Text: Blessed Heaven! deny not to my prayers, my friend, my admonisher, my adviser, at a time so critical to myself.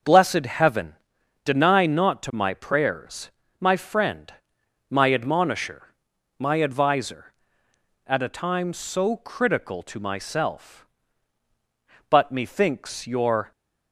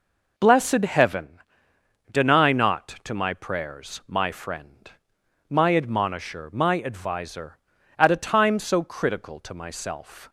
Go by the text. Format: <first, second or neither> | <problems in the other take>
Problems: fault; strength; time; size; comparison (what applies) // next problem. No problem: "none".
second | starts louder than the rest; noticeable; until 1.5 s; 6 dB // goes on to say "But methinks your"; from 12.1 s on; 1.4 s long